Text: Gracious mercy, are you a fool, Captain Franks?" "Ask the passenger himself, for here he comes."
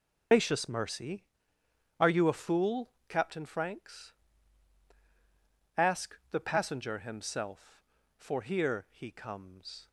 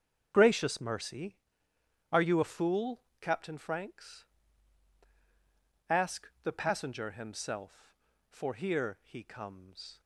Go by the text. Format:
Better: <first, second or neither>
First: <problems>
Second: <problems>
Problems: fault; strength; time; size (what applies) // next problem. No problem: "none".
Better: second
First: loses the start of "Gracious"; at 0.3 s; 95 ms // starts louder than the rest; until 2.0 s; 7 dB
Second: starts louder than the rest; strong; until 1.3 s; 7 dB